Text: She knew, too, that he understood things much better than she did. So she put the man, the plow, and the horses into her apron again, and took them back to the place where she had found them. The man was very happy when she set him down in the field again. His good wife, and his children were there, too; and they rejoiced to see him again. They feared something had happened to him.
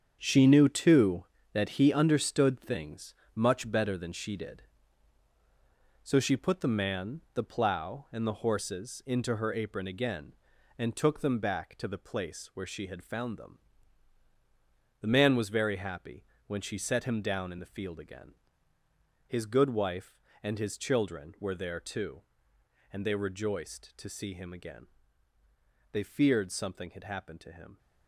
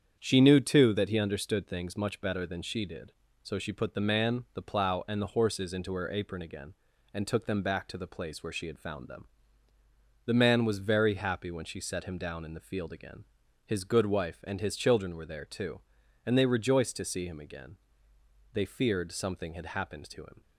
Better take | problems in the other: second | gets quieter; strong; throughout; 9.5 dB // starts louder than the rest; strong; until 1.2 s; 7.5 dB; strong in the second // pauses between "things" and "much"; slight; at 3.1 s; 0.20 s long // pauses between "happy" and "when"; slight; at 16.2 s; 0.22 s long

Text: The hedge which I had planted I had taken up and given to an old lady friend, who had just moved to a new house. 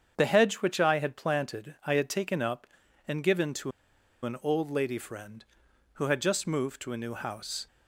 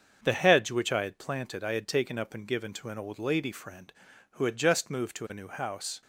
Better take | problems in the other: second | starts louder than the rest; strong; until 1.1 s; 7.5 dB; also in the second // pauses between "to" and "an"; noticeable; at 3.7 s; 0.53 s long

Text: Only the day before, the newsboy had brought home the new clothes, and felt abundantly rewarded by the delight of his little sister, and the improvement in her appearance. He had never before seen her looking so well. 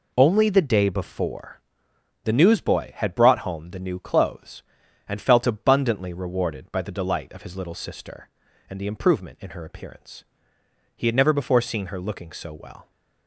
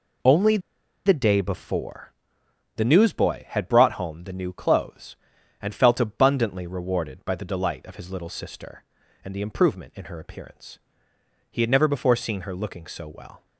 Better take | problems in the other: first | pauses between "Only" and "the"; noticeable; at 0.5 s; 0.47 s long

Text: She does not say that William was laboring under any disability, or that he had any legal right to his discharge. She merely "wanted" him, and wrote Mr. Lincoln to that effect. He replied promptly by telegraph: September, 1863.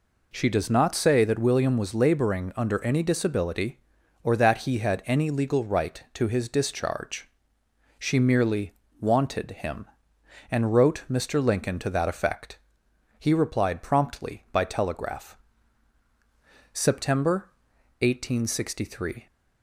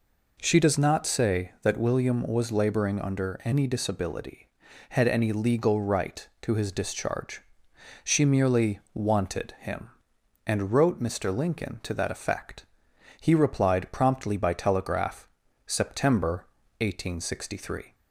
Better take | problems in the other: first | skips "or that he"; at 4.6 s // pauses between "merely" and "wanted"; slight; at 8.7 s; 0.16 s long; slight in the first

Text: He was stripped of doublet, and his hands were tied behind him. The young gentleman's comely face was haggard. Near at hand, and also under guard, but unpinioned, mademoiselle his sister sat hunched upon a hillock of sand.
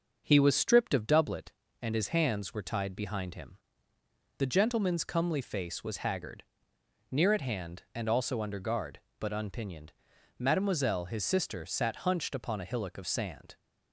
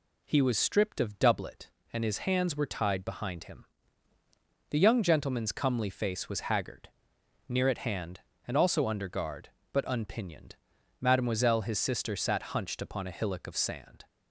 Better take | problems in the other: second | starts louder than the rest; until 1.2 s; 6.5 dB // skips "young"; at 4.4 s

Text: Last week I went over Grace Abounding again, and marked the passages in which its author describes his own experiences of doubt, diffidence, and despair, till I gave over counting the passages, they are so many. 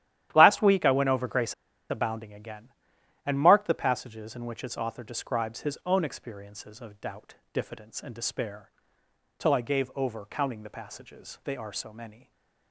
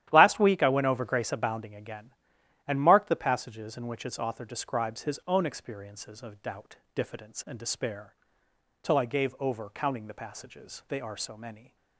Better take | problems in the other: second | starts louder than the rest; strong; until 1.3 s; 12 dB; strong in the second // pauses between "Grace" and "Abounding"; at 1.5 s; 0.36 s long // stays silent after the last word; slight; from 12.1 s on; 0.6 s long

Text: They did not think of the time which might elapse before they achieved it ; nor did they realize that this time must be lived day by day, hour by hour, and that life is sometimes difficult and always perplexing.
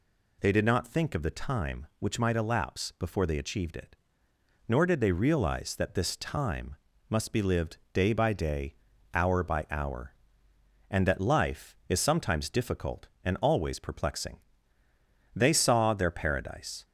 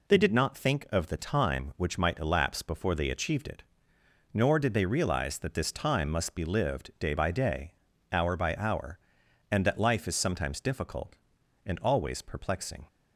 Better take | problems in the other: second | pauses between "time" and "must"; slight; at 6.7 s; 0.34 s long // goes on to say "They saw their paradise"; from 15.3 s on; 1.5 s long

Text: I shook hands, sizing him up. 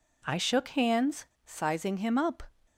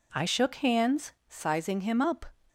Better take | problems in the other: neither | none

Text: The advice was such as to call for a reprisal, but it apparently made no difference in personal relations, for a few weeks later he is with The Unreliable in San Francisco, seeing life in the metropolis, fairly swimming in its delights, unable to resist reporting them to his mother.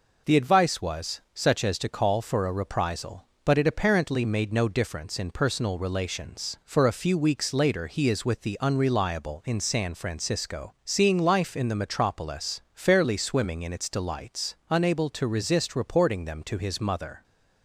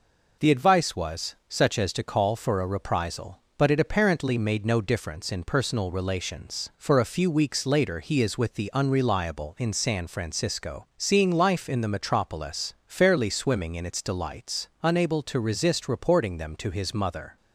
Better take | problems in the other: neither | none

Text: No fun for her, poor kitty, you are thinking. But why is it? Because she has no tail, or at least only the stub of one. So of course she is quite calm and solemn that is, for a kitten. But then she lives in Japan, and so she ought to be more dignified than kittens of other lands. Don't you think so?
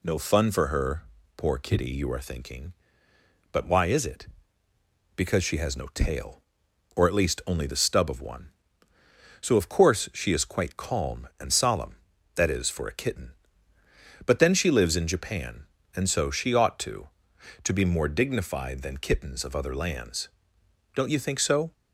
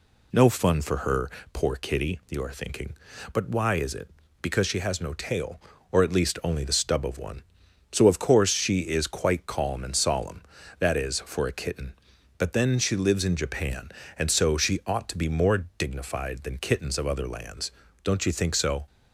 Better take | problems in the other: second | says "to" twice; at 17.6 s

